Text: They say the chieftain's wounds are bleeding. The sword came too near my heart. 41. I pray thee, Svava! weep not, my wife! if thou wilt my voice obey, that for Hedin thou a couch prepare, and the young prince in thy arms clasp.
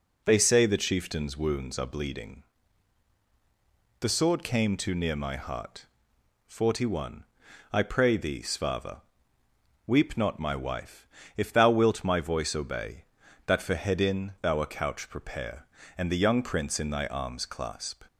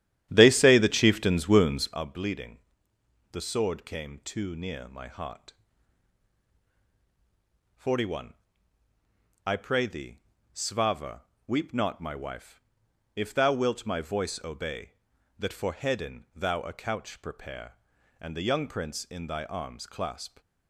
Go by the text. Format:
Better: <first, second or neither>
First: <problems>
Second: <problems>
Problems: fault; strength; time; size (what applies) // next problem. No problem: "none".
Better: first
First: none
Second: starts louder than the rest; strong; until 2.0 s; 11 dB